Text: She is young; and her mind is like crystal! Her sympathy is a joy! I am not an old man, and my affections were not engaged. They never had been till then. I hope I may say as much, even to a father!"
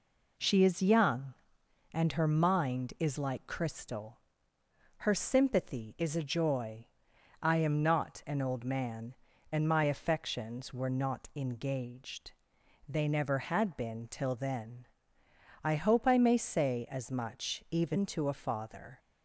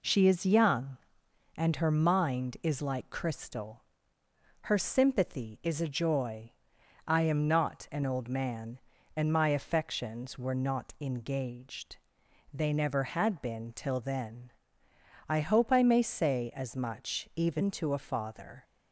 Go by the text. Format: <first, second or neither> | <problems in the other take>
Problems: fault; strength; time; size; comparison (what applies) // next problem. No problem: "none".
neither | none